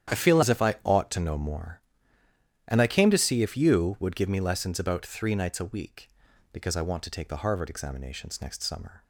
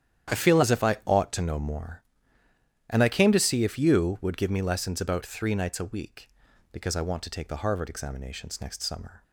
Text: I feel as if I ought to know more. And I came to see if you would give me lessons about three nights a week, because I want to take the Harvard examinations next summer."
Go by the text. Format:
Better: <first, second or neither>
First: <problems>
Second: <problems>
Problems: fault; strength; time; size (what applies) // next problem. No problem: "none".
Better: neither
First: starts louder than the rest; strong; until 1.2 s; 10 dB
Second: starts louder than the rest; strong; until 1.4 s; 10 dB